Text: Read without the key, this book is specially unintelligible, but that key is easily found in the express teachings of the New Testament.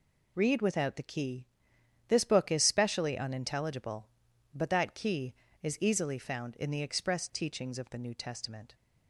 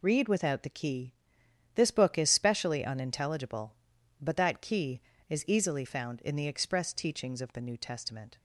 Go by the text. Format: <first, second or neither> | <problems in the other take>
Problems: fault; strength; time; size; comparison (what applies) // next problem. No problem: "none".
neither | none